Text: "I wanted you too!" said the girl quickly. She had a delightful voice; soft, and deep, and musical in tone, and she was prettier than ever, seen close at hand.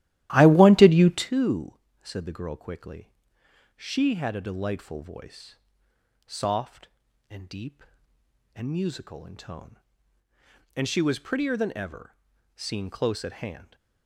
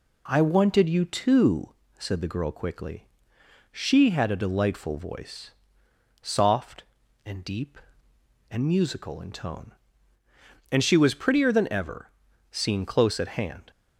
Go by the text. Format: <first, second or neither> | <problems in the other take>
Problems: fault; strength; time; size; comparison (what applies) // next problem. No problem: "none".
second | starts louder than the rest; strong; until 1.3 s; 14 dB